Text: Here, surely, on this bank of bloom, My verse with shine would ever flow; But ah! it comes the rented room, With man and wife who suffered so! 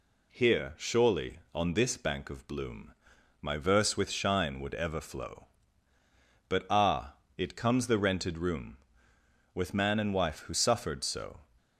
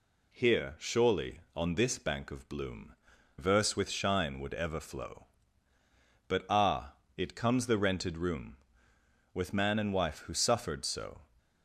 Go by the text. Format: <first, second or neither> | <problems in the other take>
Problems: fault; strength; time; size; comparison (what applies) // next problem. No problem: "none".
first | skips "My"; at 3.1 s